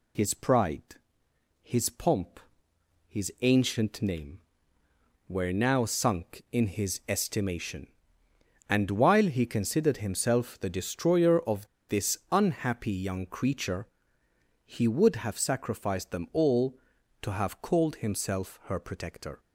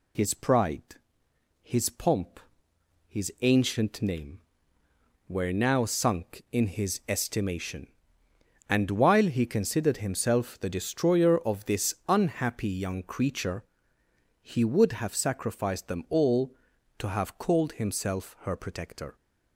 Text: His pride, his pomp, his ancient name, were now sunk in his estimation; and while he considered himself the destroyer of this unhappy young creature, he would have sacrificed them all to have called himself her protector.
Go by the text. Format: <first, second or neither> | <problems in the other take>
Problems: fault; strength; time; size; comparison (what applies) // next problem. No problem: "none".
second | pauses between "of" and "this"; slight; at 11.6 s; 0.22 s long